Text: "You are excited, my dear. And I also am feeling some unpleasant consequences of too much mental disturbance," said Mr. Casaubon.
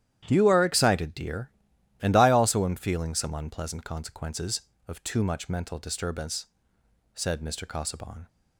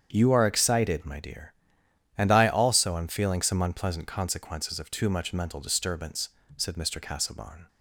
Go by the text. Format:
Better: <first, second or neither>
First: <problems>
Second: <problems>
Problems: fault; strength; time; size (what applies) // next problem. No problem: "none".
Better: second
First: starts louder than the rest; strong; until 1.3 s; 11 dB // skips "my"; at 1.1 s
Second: starts louder than the rest; strong; until 1.1 s; 8 dB